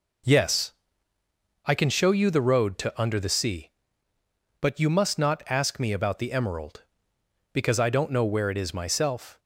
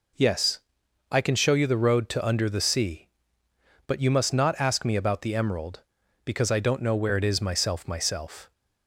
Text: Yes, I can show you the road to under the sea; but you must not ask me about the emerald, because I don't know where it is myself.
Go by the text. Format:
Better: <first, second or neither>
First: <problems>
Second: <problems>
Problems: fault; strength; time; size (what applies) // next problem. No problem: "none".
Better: first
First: none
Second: says "myself" twice; at 7.8 s